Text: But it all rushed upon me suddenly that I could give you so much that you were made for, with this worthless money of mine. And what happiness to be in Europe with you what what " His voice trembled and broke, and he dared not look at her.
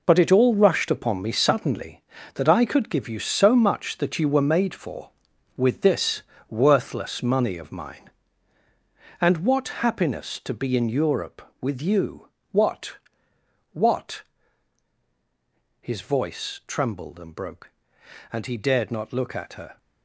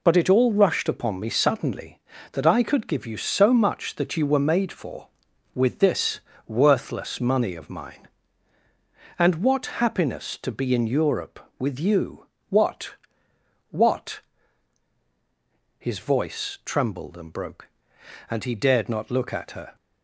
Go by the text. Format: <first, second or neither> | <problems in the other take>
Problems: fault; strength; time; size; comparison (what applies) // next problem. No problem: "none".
second | gets quieter; strong; throughout; 17.5 dB // pauses between "this" and "worthless"; slight; at 6.2 s; 0.28 s long; slight in the second // pauses between "you" and "what"; slight; at 12.2 s; 0.24 s long; slight in the second // pauses between "what" and "what"; noticeable; at 12.9 s; 0.74 s long; noticeable in the second